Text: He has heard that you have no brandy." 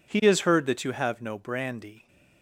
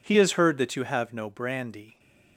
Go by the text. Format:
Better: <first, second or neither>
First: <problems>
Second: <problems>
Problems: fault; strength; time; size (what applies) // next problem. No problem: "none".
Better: neither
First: none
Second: none